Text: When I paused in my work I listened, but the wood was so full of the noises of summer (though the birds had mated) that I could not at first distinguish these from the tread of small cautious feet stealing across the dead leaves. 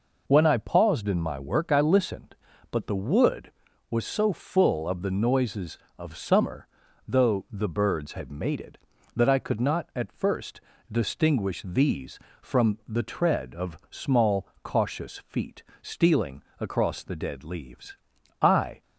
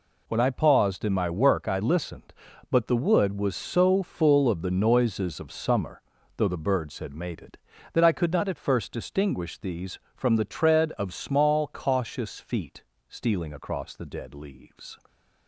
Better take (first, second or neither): second